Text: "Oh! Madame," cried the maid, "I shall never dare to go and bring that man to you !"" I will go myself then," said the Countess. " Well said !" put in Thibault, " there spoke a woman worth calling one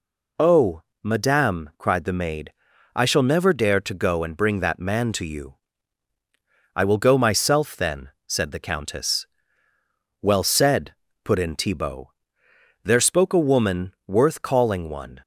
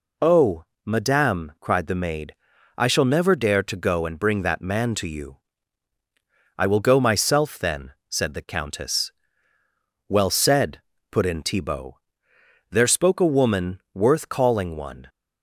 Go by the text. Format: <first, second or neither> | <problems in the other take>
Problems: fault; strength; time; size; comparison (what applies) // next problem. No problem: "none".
neither | none